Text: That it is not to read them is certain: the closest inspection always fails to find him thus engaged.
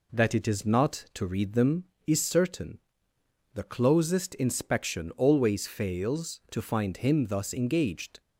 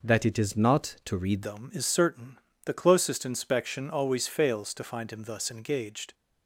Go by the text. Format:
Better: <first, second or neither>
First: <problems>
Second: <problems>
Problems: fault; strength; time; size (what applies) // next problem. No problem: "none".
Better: first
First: none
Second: changes voice at "them"; from 1.4 s on; 4.7 s long